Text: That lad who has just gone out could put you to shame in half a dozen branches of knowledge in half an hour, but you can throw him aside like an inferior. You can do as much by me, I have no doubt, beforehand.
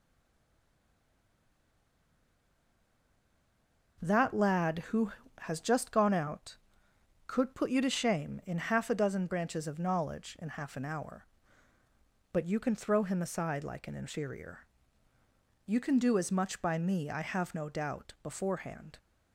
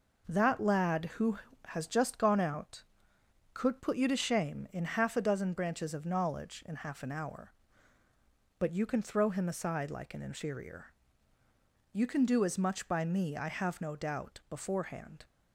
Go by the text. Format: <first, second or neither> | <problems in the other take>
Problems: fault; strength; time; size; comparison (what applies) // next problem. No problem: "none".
second | stays silent before the first word; strong; until 3.9 s; 3.9 s long